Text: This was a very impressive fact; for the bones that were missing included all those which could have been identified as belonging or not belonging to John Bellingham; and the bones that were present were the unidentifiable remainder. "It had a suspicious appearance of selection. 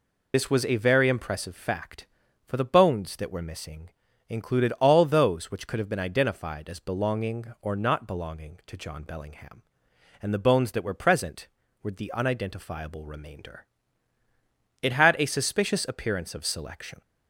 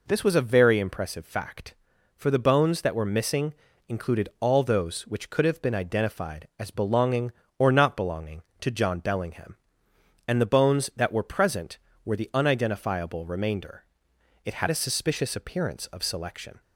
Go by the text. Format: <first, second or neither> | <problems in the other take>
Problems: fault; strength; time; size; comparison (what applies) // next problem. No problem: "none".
second | loses the start of "This"; at 0.3 s; 30 ms // pauses between "missing" and "included"; at 3.8 s; 0.40 s long; slight in the second